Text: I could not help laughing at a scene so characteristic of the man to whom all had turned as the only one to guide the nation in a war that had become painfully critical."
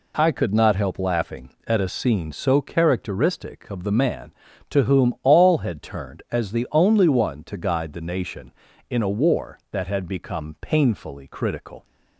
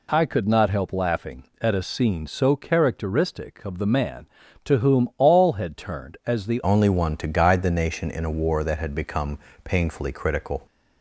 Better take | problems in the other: first | changes voice at "only"; from 6.6 s on; 4.0 s long // pauses between "become" and "painfully"; slight; at 9.3 s; 0.28 s long

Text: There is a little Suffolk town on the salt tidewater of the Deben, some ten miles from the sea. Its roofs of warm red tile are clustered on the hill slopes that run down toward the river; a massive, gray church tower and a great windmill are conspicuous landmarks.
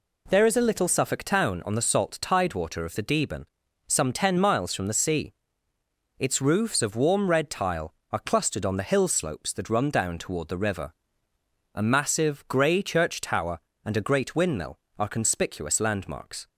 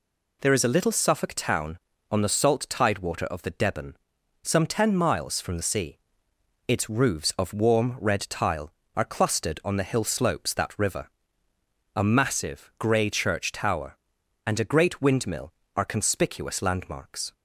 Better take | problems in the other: first | skips "run down toward the"; at 10.7 s

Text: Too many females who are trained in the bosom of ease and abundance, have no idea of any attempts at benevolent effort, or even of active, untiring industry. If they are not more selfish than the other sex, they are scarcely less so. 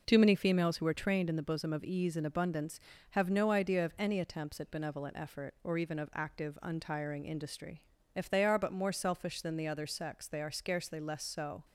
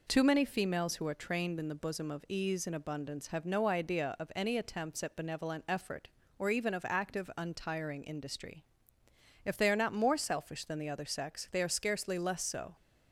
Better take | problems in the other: second | says "but" for "not"; at 8.5 s

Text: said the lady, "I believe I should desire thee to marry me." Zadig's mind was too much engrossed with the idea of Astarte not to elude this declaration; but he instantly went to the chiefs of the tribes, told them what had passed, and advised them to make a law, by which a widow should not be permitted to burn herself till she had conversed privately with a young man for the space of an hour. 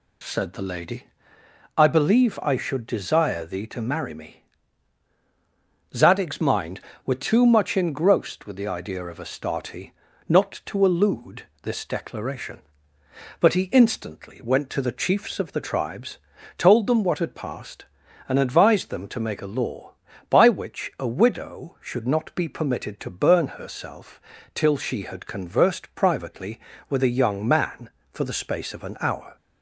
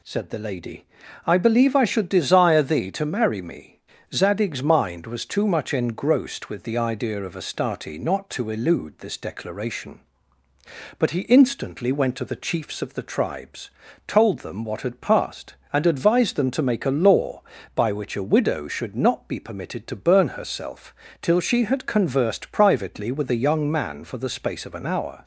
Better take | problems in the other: second | says "were" for "was"; at 7.0 s // pauses between "Astarte" and "not"; at 9.9 s; 0.38 s long // pauses between "elude" and "this"; slight; at 11.4 s; 0.18 s long // pauses between "herself" and "till"; slight; at 24.2 s; 0.34 s long; slight in the second

